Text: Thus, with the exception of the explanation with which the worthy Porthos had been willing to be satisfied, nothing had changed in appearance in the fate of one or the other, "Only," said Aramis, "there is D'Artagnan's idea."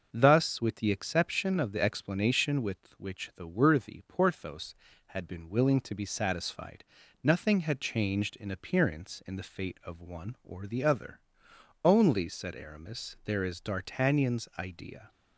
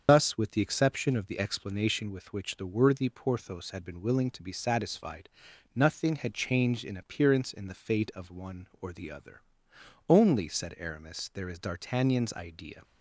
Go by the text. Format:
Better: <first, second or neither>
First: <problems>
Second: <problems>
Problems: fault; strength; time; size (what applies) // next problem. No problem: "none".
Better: first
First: none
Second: loses the start of "Thus"; at 0.0 s; 115 ms // starts louder than the rest; until 1.0 s; 7 dB